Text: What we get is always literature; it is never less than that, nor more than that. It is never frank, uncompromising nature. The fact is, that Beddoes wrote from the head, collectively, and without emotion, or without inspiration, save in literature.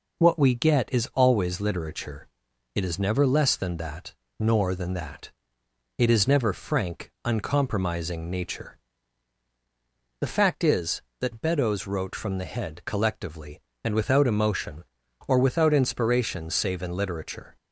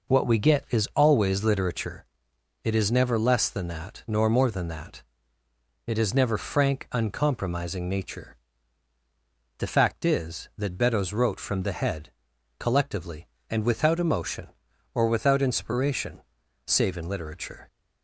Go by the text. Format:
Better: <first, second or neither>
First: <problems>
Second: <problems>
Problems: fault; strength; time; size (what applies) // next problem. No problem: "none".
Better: second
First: skips "more"; at 4.7 s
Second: none